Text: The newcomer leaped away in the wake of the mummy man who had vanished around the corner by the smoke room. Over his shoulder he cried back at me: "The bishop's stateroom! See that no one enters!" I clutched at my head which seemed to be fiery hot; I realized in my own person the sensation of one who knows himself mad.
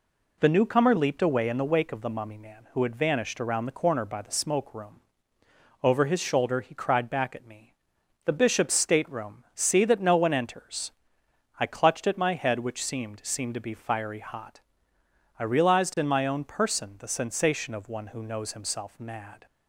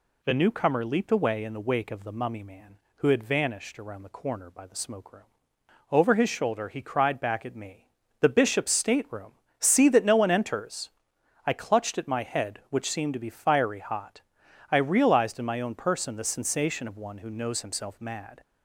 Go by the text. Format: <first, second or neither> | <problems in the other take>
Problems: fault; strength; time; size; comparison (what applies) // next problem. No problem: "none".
second | says "seemed" twice; at 13.2 s